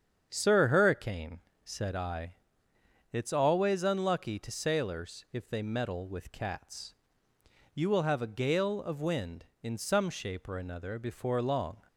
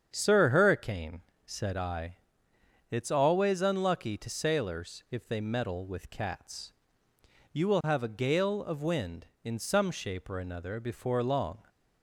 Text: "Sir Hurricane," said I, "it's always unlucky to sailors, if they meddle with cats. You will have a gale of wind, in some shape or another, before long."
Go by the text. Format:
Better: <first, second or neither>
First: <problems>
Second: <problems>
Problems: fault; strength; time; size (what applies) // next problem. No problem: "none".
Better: neither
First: starts louder than the rest; strong; until 1.3 s; 8 dB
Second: starts louder than the rest; strong; until 1.1 s; 8 dB